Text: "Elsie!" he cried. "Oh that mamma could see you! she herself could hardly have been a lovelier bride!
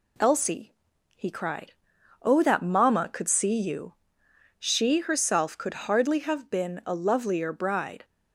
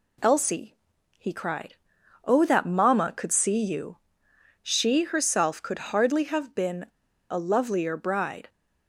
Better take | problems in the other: first | pauses between "been" and "a"; at 6.8 s; 0.45 s long

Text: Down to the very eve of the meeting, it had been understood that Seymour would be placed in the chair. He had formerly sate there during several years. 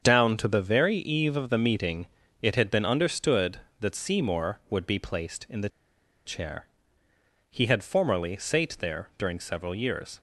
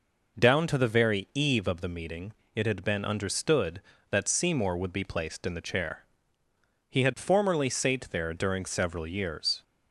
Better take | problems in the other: second | starts louder than the rest; strong; until 1.0 s; 7 dB // pauses between "the" and "chair"; noticeable; at 5.6 s; 0.56 s long

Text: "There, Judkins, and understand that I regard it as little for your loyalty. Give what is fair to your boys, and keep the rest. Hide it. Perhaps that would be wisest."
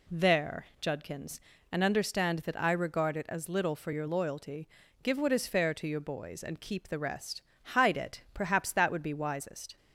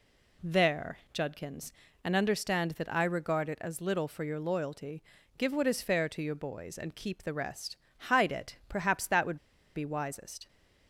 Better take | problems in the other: first | pauses between "would" and "be"; at 9.3 s; 0.36 s long

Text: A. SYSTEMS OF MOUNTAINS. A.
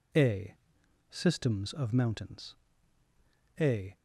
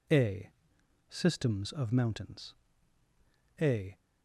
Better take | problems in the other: neither | none

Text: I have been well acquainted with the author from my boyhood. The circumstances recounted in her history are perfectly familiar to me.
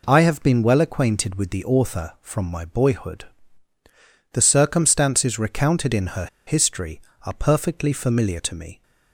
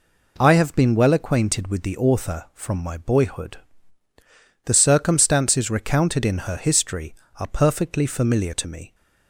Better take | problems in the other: second | pauses between "her" and "history"; slight; at 6.2 s; 0.20 s long

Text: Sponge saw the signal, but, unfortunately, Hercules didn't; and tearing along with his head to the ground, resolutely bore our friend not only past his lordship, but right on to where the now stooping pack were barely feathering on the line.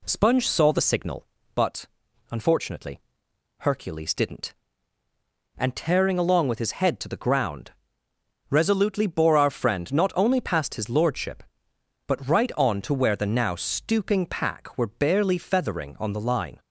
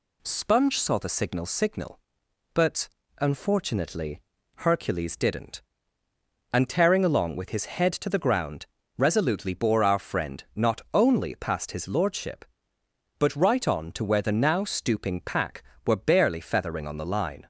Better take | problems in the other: first | says "signal" twice; at 1.4 s

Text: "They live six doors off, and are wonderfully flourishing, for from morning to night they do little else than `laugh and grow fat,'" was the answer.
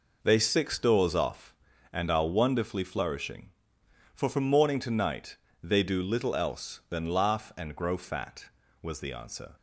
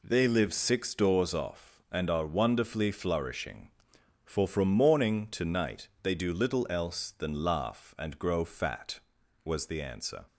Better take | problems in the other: second | skips "live"; at 0.3 s // pauses between "night" and "they"; slight; at 5.3 s; 0.26 s long

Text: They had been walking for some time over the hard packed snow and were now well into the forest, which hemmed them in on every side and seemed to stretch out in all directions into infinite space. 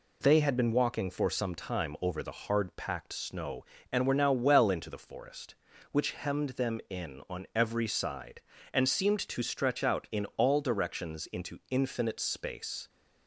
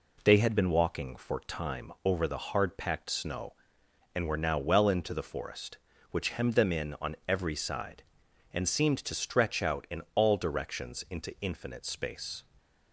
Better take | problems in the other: first | skips "some"; at 1.3 s

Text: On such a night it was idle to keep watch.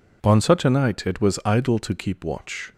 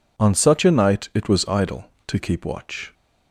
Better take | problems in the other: neither | none

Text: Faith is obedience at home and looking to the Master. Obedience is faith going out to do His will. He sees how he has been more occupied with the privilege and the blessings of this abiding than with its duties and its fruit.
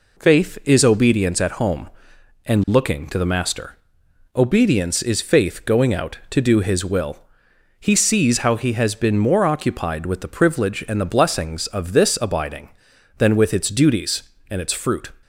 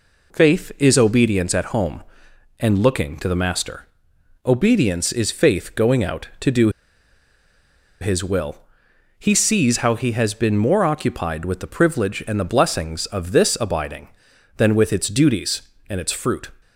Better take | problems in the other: first | pauses between "do" and "His"; strong; at 6.6 s; 1.3 s long

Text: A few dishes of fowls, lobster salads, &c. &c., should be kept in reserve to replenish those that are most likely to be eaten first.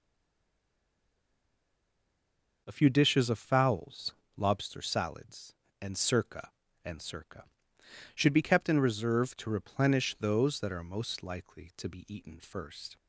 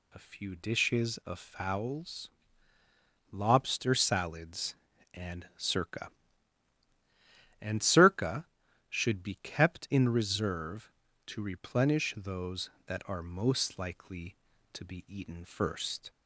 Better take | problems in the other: second | stays silent before the first word; strong; until 2.6 s; 2.6 s long

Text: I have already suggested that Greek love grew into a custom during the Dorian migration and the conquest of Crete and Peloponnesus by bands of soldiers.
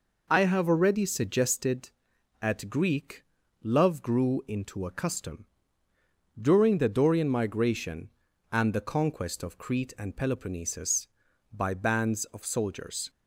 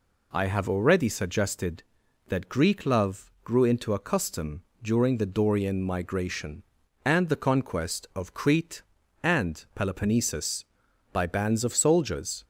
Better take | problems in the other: second | says "at" for "that"; at 2.4 s // pauses between "Greek" and "love"; at 3.2 s; 0.40 s long // pauses between "custom" and "during"; noticeable; at 5.4 s; 0.94 s long; slight in the second

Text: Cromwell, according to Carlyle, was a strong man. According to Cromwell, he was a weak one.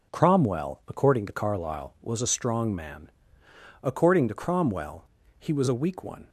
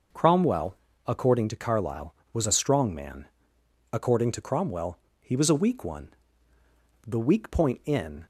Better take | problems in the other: first | goes on to say "The weak point in"; noticeable; from 7.0 s on; 1.1 s long

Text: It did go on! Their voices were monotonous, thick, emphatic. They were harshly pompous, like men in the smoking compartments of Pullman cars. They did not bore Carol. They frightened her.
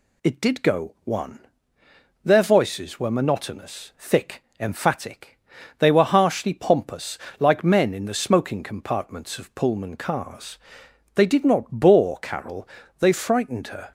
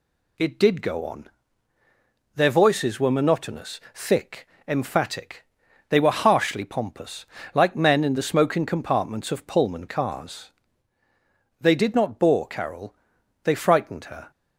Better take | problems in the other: second | says "one" for "on"; at 1.0 s

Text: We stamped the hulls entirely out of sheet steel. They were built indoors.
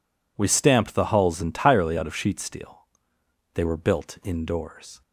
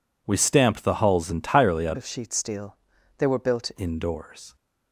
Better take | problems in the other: first | changes voice from "of" to "built"; from 1.9 to 3.7 s; 1.8 s long

